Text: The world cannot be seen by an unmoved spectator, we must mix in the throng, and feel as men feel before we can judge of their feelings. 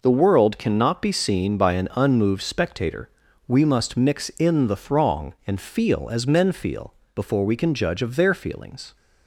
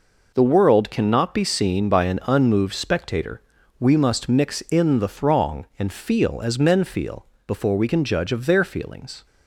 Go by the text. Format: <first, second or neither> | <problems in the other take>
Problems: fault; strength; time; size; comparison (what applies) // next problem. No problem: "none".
neither | pauses between "feel" and "before"; slight; the same in both